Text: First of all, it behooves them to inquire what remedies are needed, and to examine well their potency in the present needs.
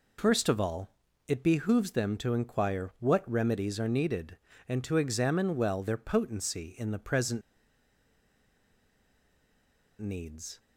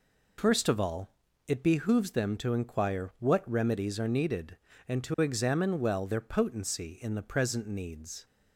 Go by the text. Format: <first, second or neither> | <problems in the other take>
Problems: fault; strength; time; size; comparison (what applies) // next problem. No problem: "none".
second | pauses between "present" and "needs"; strong; at 7.4 s; 2.5 s long